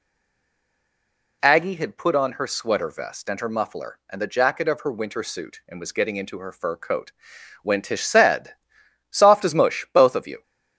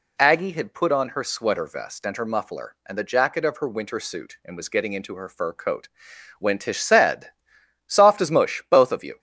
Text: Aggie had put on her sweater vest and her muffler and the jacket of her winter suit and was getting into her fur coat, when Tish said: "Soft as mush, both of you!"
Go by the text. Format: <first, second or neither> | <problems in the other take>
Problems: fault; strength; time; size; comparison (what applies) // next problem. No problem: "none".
second | stays silent before the first word; noticeable; until 1.4 s; 1.4 s long